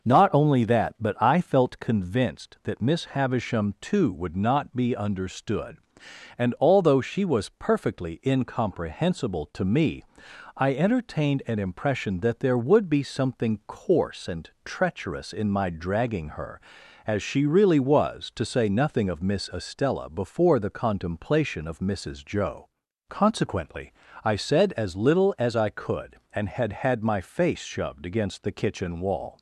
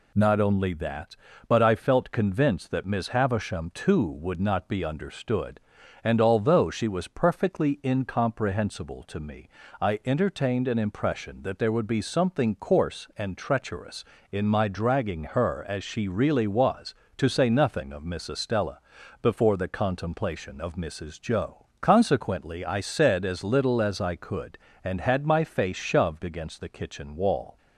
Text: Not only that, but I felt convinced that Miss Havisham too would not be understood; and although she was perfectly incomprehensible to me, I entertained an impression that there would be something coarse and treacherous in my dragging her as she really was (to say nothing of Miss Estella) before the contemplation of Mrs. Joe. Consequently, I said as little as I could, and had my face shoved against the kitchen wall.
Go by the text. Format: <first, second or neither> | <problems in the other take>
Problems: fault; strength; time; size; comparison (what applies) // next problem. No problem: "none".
second | pauses between "and" and "treacherous"; slight; at 14.4 s; 0.16 s long // says "had" twice; at 26.7 s